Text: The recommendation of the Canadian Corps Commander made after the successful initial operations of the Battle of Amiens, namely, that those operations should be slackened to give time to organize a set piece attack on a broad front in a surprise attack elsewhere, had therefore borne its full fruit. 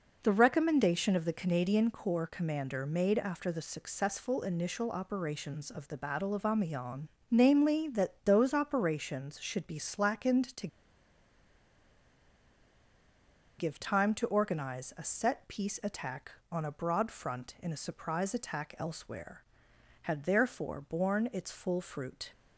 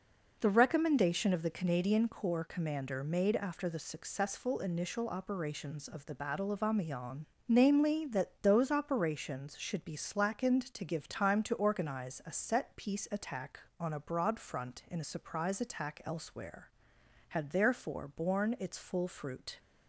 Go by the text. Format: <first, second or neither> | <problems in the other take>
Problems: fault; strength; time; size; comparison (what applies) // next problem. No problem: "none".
second | pauses between "to" and "give"; strong; at 10.6 s; 2.9 s long